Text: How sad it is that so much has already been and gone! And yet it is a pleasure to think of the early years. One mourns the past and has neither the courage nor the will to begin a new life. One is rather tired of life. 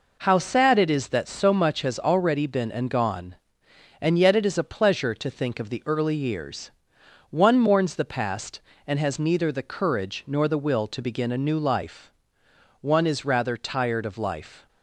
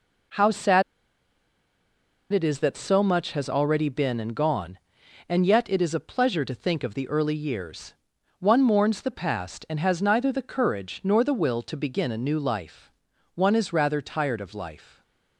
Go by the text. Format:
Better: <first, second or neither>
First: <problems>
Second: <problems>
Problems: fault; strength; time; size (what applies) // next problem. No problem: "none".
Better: first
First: none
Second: pauses between "sad" and "it"; strong; at 0.8 s; 1.4 s long